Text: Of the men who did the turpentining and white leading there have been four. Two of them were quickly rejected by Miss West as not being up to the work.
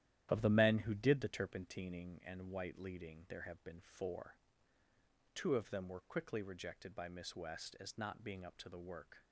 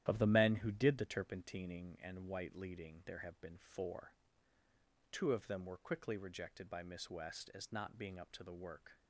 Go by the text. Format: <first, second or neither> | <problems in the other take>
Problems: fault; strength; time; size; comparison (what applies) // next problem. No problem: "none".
neither | starts louder than the rest; strong; the same in both